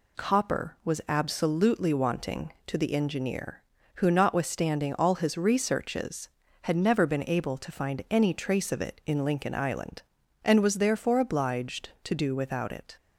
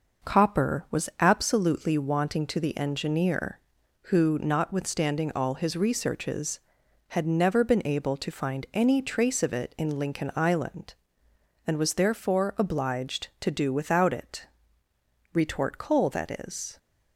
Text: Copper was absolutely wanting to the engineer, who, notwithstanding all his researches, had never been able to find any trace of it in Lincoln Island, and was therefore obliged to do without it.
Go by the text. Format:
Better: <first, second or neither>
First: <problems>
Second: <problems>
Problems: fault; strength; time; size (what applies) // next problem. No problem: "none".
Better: first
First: none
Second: goes on to say "Retort coal that is"; from 15.3 s on; 1.4 s long